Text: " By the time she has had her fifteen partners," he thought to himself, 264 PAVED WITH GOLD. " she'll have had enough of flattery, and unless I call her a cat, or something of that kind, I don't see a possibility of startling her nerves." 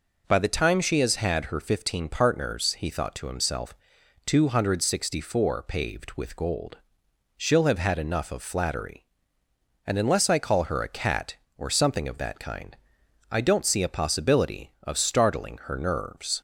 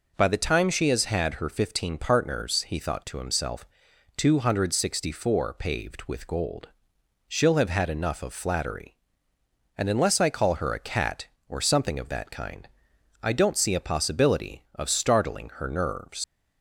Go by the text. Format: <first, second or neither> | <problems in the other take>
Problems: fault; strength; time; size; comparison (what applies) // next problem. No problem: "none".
first | leaves "nerves" unfinished; at 16.2 s; 85 ms